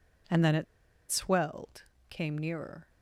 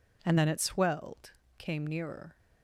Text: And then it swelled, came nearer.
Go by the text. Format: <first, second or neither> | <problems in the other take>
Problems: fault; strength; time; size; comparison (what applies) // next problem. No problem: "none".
second | pauses between "it" and "swelled"; noticeable; at 0.6 s; 0.46 s long